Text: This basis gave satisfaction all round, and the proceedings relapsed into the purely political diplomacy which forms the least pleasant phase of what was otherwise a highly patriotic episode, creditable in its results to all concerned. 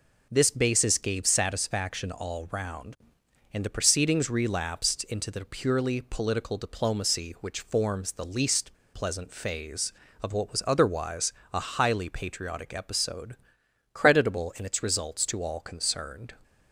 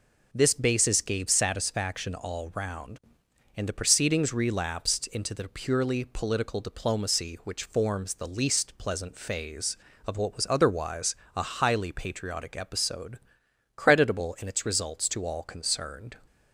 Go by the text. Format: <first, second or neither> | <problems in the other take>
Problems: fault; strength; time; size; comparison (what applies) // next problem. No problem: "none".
second | pauses between "least" and "pleasant"; slight; at 8.7 s; 0.18 s long // pauses between "otherwise" and "a"; slight; at 11.3 s; 0.22 s long; slight in the second